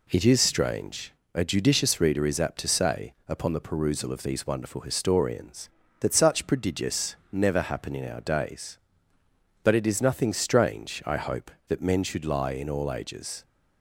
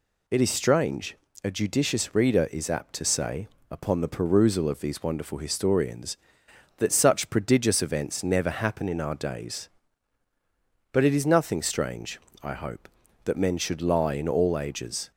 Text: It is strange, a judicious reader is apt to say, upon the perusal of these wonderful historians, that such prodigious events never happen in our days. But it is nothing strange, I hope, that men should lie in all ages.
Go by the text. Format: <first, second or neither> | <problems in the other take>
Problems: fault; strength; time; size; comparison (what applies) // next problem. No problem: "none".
second | skips "events"; at 7.2 s